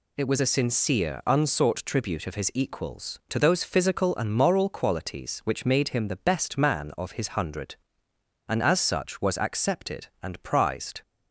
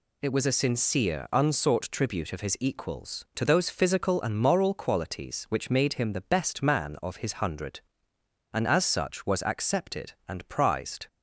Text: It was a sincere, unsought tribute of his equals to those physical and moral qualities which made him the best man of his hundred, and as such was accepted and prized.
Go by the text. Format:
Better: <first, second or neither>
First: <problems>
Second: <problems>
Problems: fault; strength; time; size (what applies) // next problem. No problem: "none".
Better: neither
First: none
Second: none